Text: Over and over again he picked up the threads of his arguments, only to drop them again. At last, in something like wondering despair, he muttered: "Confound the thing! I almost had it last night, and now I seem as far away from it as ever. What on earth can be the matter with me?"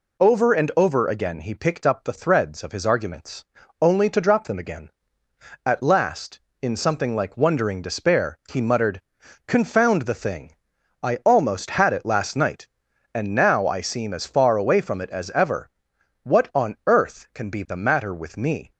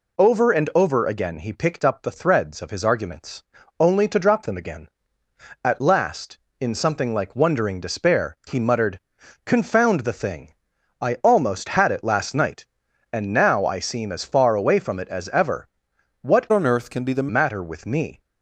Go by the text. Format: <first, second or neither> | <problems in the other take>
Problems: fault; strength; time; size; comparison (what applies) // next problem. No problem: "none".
first | changes voice from "on" to "the"; from 16.5 to 17.2 s; 0.7 s long